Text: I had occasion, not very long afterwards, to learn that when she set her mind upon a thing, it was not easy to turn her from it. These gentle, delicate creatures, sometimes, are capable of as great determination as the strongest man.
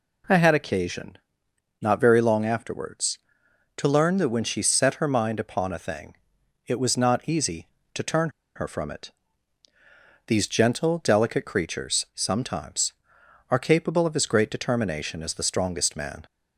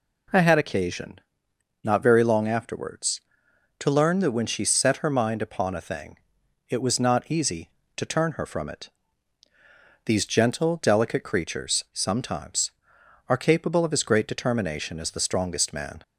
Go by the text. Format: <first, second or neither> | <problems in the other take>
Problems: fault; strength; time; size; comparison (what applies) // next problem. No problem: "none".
second | pauses between "turn" and "her"; slight; at 8.2 s; 0.26 s long